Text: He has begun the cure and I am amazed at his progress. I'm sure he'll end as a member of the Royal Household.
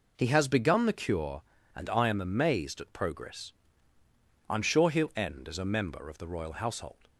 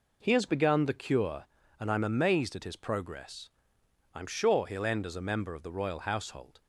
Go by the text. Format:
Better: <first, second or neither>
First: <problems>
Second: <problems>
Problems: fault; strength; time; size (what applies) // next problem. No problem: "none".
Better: second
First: skips "his"; at 2.9 s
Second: none